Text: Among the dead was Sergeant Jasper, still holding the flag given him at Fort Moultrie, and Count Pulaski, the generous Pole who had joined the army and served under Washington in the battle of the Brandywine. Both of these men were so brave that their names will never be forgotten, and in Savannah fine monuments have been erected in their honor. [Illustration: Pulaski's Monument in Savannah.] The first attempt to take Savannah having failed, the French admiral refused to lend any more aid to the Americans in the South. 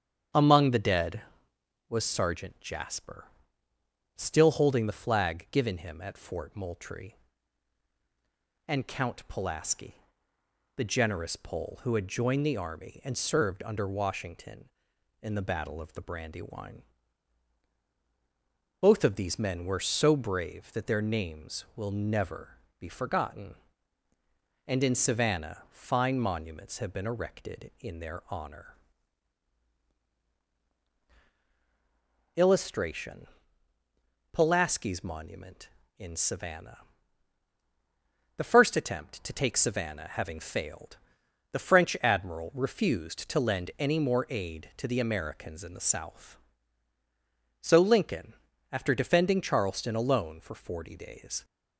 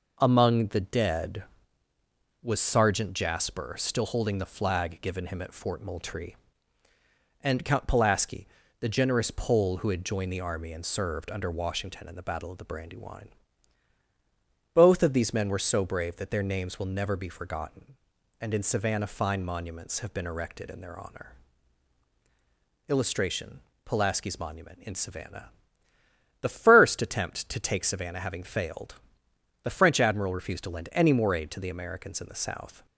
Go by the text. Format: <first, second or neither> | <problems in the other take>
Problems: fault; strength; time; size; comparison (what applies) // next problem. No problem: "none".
second | starts louder than the rest; strong; until 2.0 s; 8.5 dB // pauses between "never" and "be"; slight; at 22.5 s; 0.20 s long // goes on to say "So Lincoln after defending Charleston alone for forty days"; strong; from 47.6 s on; 3.8 s long